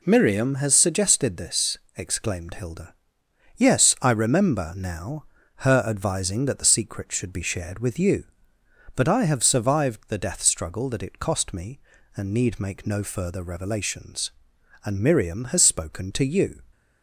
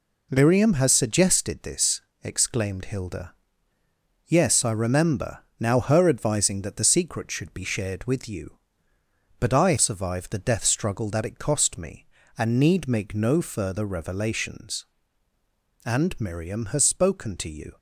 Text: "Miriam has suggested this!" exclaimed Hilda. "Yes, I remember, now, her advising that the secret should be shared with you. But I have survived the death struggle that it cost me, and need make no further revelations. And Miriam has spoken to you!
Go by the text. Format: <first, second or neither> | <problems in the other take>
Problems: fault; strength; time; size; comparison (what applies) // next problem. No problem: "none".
first | skips "have"; at 9.7 s